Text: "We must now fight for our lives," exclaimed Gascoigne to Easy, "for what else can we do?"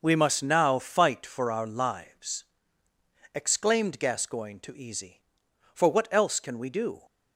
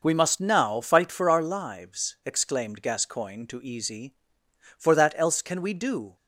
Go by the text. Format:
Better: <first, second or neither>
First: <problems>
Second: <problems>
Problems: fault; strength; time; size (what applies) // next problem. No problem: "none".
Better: first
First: none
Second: says "that" for "what"; at 4.9 s